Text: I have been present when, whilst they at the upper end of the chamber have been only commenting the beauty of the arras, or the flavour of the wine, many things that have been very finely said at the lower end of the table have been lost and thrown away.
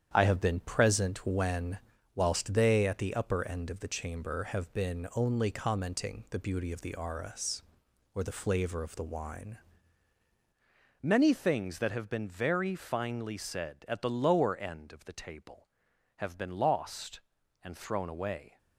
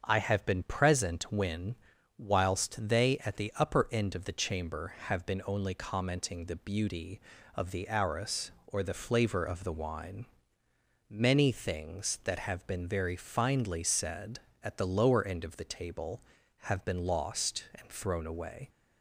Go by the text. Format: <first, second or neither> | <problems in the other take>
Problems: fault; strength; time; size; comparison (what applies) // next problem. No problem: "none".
second | starts louder than the rest; strong; until 1.1 s; 9 dB; also in the second // changes voice at "many"; from 11.0 s on; 7.5 s long